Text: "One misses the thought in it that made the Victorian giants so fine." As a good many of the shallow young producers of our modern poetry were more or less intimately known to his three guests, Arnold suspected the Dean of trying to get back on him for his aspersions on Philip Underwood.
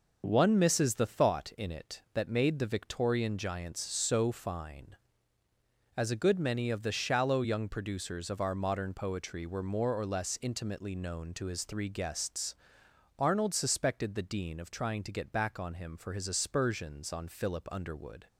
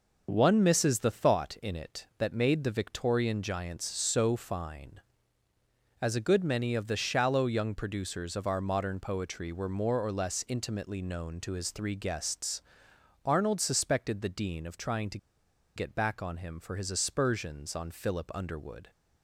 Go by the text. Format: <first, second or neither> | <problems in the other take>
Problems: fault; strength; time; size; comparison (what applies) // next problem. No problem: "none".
first | pauses between "to" and "get"; noticeable; at 15.1 s; 0.58 s long